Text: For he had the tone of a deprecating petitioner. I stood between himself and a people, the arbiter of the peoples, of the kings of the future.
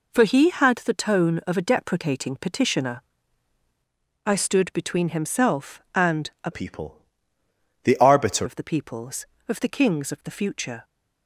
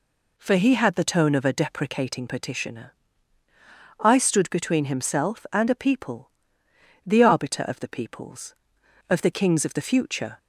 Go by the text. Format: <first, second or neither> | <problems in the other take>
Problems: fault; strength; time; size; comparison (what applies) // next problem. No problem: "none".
second | pauses between "and" and "a"; slight; at 6.2 s; 0.16 s long // changes voice from "people" to "arbiter"; from 6.5 to 8.4 s; 1.9 s long